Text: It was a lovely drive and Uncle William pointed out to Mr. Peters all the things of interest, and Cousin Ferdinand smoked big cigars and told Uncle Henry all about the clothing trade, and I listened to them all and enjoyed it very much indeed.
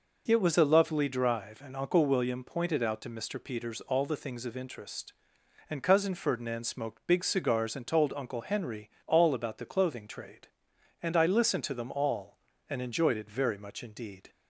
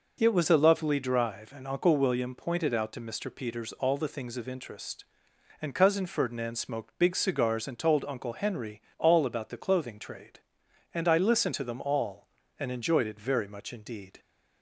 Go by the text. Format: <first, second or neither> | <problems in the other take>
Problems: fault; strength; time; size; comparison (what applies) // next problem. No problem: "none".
neither | pauses between "Henry" and "all"; slight; the same in both